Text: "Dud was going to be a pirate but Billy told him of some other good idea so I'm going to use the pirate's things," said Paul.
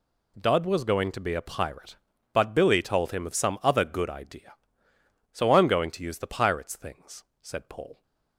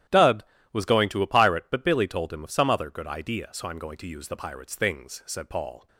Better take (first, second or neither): first